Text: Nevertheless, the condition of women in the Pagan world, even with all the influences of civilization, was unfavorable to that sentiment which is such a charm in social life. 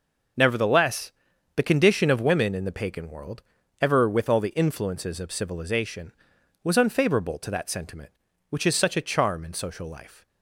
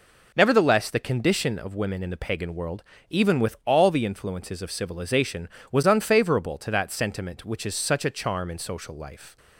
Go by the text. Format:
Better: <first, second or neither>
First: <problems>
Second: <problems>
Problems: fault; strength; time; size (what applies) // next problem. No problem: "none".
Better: second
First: says "ever" for "even"; at 3.7 s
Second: none